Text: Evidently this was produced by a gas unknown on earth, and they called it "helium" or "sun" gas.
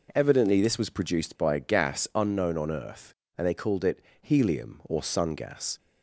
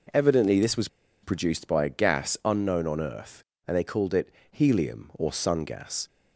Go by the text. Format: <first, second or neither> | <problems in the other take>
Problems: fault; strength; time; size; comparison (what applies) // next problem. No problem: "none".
first | pauses between "was" and "produced"; slight; at 0.8 s; 0.35 s long // pauses between "it" and "helium"; slight; at 4.3 s; 0.20 s long; slight in the first